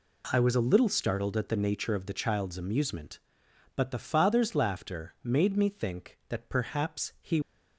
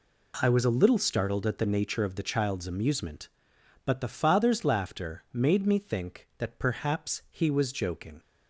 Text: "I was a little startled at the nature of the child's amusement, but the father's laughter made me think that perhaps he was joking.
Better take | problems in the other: second | stops before "was joking"; at 7.4 s

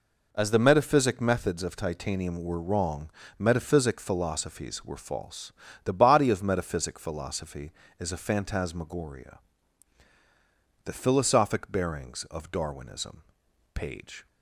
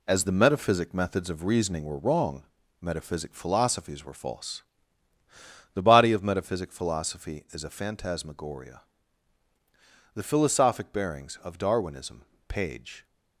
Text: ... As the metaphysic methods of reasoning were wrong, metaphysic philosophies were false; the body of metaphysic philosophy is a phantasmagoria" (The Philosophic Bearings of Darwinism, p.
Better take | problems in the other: second | says "titanium" for "reasoning"; at 1.7 s

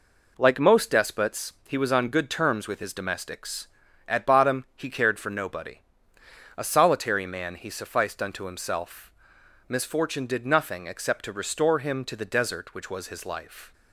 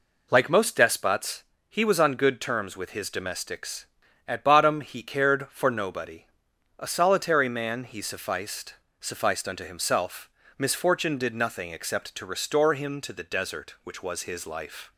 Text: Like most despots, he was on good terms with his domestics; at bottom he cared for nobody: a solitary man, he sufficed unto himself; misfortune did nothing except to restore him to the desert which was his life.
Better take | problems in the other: first | says "sufficed" twice; at 8.9 s

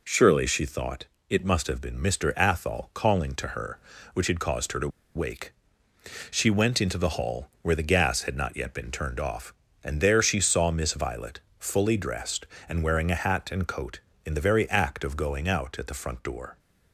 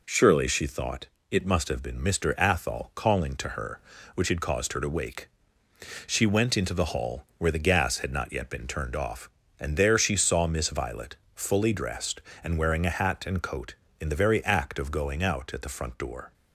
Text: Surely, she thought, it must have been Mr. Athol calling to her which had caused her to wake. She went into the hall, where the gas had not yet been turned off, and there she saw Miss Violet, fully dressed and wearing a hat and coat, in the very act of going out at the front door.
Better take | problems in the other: second | pauses between "to" and "wake"; slight; at 4.8 s; 0.27 s long

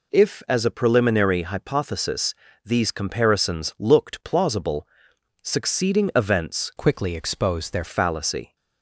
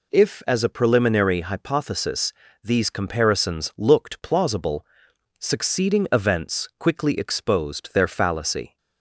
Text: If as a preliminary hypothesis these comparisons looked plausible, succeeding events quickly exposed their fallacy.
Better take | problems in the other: second | pauses between "hypothesis" and "these"; slight; at 2.3 s; 0.32 s long; slight in the second // changes voice from "quickly" to "their"; from 6.7 to 7.8 s; 1.1 s long

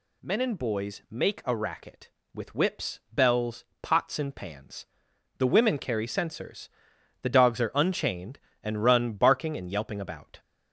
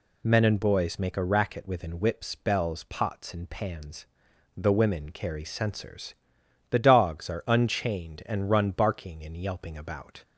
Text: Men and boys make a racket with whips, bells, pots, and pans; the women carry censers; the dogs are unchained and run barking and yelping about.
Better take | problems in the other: first | says "within" for "with"; at 1.6 s

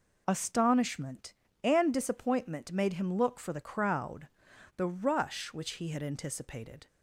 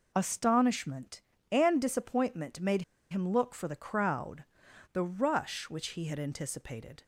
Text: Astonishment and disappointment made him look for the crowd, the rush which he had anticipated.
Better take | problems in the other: first | pauses between "made" and "him"; slight; at 2.8 s; 0.28 s long

